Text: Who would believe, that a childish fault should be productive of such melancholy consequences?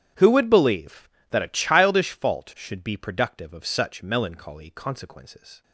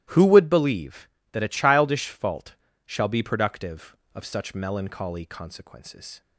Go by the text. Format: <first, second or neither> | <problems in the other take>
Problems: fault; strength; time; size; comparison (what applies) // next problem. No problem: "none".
first | starts louder than the rest; strong; until 1.3 s; 14.5 dB; strong in the first // says "shall" for "should"; at 2.8 s